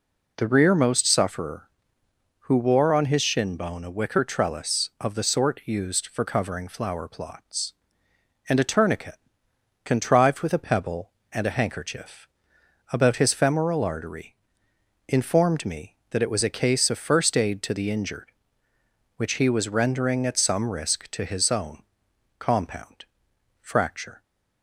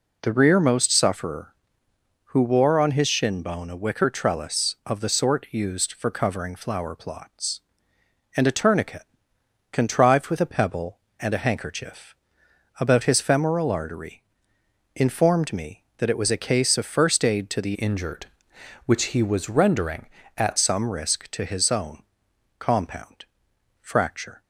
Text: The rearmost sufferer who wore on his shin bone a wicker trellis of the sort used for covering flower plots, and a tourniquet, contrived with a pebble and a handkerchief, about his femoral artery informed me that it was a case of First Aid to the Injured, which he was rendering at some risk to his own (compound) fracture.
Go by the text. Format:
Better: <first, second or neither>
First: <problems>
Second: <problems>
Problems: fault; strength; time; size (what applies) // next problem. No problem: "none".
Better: first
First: pauses between "artery" and "informed"; noticeable; at 14.3 s; 0.72 s long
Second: pauses between "artery" and "informed"; noticeable; at 14.2 s; 0.72 s long // changes voice from "Injured" to "at"; from 17.7 to 20.5 s; 2.8 s long